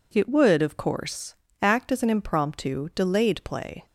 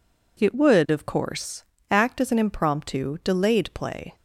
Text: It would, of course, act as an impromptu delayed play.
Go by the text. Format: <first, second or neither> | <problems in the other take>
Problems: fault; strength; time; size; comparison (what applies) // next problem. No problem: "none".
neither | none